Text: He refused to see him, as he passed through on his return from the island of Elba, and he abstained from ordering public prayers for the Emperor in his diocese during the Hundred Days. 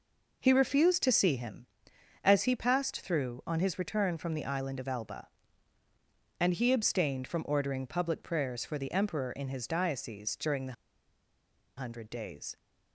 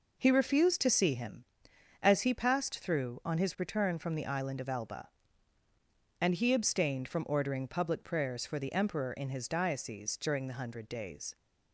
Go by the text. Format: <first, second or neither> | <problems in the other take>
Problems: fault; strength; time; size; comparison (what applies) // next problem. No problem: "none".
second | pauses between "the" and "Hundred"; at 10.7 s; 1.0 s long